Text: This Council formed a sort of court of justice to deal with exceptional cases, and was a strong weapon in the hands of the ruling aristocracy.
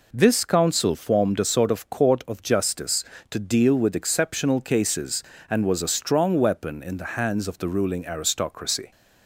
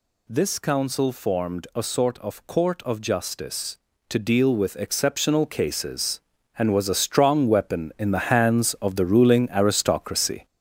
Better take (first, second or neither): first